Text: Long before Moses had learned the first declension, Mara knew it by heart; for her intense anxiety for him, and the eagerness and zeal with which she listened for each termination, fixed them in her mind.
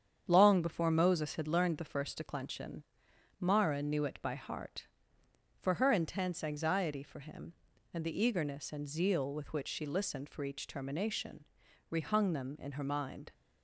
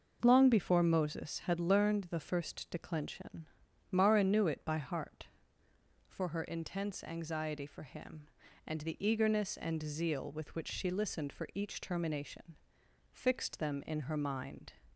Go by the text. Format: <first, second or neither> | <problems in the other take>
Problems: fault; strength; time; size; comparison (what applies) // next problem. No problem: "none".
second | starts louder than the rest; strong; until 1.2 s; 8 dB // says "rehung" for "fixed"; at 11.9 s